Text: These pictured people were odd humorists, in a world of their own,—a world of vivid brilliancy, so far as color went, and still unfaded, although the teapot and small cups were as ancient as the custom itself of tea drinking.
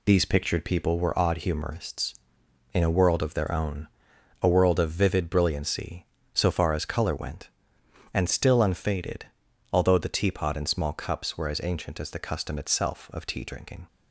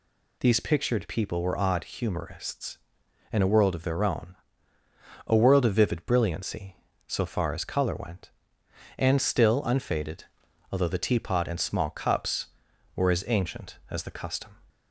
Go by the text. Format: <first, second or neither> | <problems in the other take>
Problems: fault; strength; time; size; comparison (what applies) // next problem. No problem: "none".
first | stops before "itself of tea drinking"; at 14.7 s